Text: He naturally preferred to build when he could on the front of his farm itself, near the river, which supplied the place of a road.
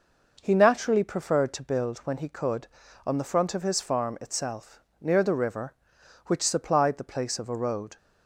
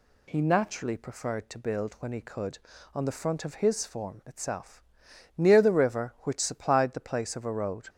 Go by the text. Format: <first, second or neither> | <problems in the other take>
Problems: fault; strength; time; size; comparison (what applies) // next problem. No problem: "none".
first | says "form" for "farm"; at 3.8 s